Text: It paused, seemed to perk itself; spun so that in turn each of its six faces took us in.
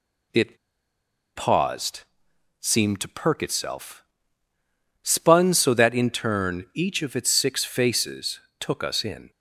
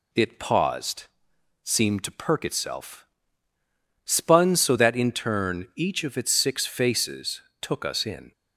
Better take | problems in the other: second | pauses between "It" and "paused"; noticeable; at 0.5 s; 0.78 s long // pauses between "faces" and "took"; slight; at 8.4 s; 0.18 s long; slight in the second

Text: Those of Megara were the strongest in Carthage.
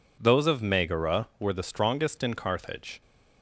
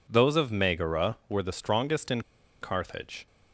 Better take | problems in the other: first | pauses between "in" and "Carthage"; at 2.2 s; 0.39 s long

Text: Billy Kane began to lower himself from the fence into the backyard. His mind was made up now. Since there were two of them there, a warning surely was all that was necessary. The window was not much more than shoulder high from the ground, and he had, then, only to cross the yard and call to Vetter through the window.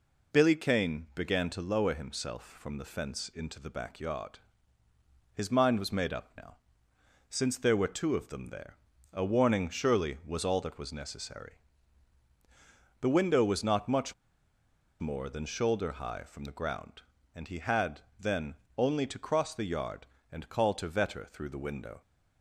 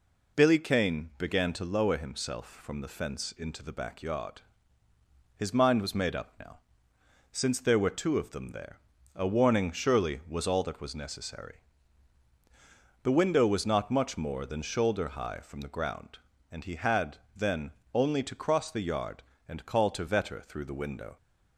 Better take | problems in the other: second | pauses between "much" and "more"; noticeable; at 14.1 s; 0.87 s long

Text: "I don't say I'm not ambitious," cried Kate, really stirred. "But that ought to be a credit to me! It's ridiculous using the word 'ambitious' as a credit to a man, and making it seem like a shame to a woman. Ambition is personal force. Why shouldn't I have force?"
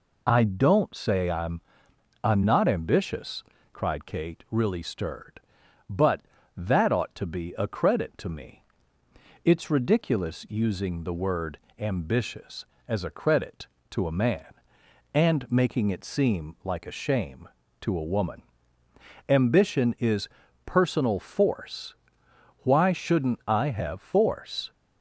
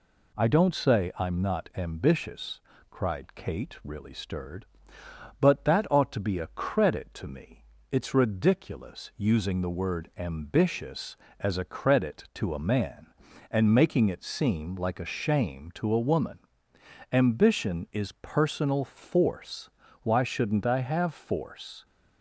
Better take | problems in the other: second | says "I'm" twice; at 2.2 s // pauses between "word" and "ambitious"; slight; at 11.5 s; 0.18 s long // pauses between "is" and "personal"; slight; at 20.2 s; 0.36 s long

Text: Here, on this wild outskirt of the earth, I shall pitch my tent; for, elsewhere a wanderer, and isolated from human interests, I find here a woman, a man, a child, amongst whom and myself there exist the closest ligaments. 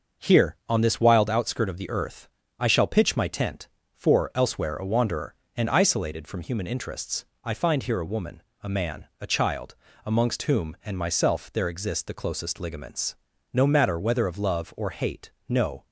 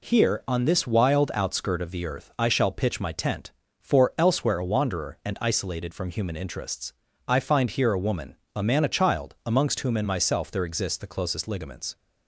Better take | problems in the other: second | starts louder than the rest; noticeable; until 1.3 s; 6 dB // goes on to say "No matter whether of love or hate no"; strong; from 13.5 s on; 2.3 s long

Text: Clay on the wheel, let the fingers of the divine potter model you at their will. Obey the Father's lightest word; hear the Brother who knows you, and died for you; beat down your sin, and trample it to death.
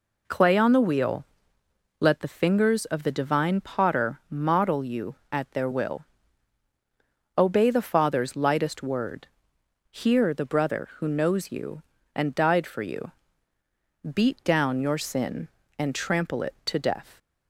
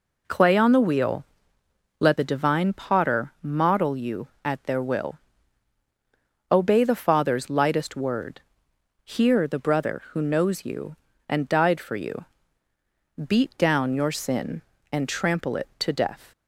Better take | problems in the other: first | skips "the fingers of"; at 2.1 s

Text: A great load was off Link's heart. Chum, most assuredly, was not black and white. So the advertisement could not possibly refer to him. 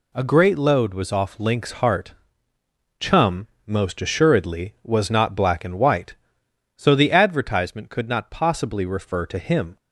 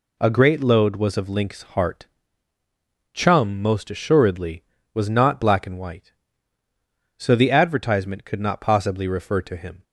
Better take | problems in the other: first | says "of" for "off"; at 1.1 s

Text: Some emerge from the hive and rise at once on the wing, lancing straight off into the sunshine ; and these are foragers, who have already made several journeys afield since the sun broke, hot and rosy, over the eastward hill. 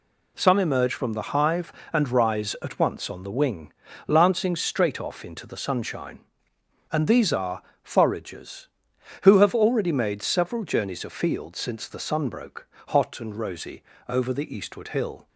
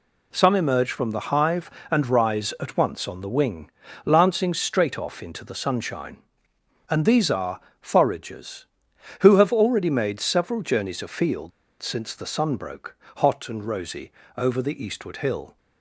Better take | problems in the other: first | pauses between "are" and "foragers"; slight; at 7.5 s; 0.22 s long; slight in the first // pauses between "afield" and "since"; slight; at 11.5 s; 0.29 s long

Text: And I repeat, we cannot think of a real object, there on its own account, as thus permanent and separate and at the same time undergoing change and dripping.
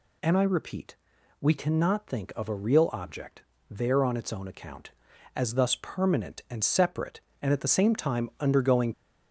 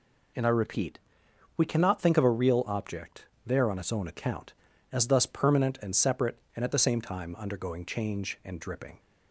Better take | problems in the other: second | stops before "change and dripping"; at 8.9 s

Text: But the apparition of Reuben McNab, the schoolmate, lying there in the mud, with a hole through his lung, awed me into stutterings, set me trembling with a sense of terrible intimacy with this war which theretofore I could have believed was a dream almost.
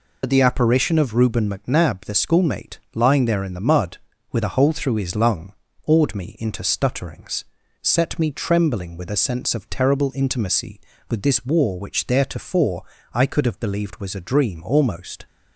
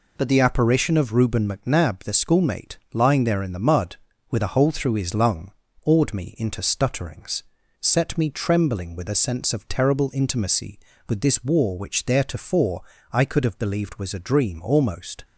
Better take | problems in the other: second | loses the start of "But"; at 0.2 s; 55 ms // pauses between "theretofore" and "I"; slight; at 12.8 s; 0.32 s long; slight in the second

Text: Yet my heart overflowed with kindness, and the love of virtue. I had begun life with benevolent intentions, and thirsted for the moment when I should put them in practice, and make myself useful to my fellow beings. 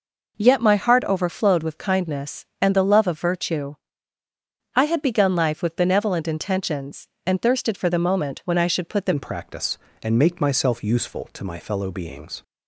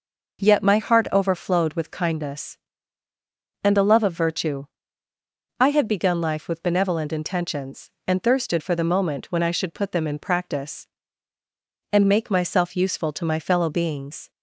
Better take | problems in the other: second | changes voice at "in"; from 9.1 s on; 3.3 s long

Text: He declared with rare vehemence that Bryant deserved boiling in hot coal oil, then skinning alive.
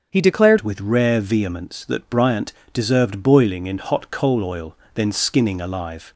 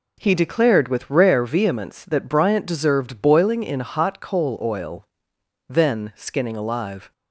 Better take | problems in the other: second | starts louder than the rest; until 1.1 s; 6.5 dB // changes voice at "with"; from 0.6 s on; 5.5 s long // pauses between "Bryant" and "deserved"; slight; at 2.5 s; 0.20 s long

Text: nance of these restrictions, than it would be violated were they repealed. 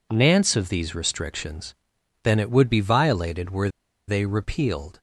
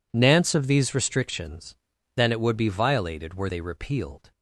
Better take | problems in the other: second | pauses between "were" and "they"; at 3.6 s; 0.39 s long

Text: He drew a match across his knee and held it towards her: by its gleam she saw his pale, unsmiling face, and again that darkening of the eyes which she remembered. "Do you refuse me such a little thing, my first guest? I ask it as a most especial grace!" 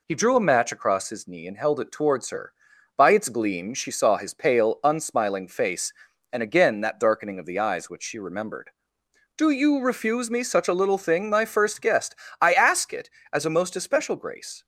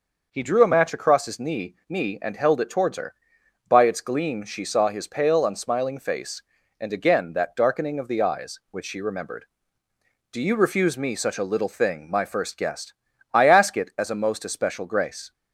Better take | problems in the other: first | says "knee" twice; at 1.8 s

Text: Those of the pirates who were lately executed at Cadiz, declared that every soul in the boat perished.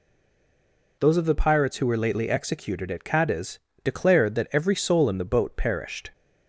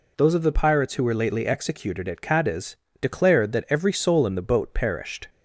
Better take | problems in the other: second | stays silent before the first word; until 0.9 s; 0.9 s long

